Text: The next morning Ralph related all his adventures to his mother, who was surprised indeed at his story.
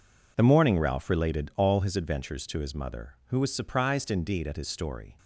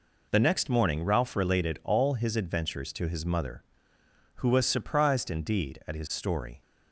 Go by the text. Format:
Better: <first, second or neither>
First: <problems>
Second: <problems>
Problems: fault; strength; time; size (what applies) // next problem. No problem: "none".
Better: second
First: skips "next"; at 0.4 s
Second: none